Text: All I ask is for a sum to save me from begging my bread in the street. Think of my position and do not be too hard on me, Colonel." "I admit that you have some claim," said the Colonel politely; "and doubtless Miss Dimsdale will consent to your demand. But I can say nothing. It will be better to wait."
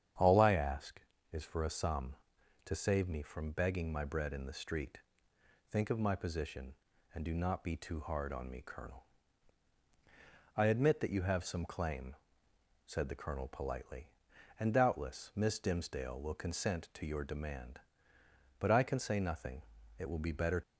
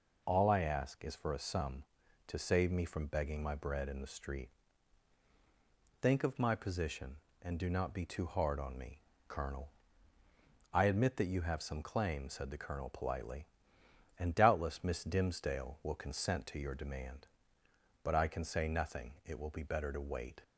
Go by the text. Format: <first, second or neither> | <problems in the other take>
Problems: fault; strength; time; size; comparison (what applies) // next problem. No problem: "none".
second | starts louder than the rest; strong; until 1.5 s; 9 dB // stops before "to wait"; at 20.6 s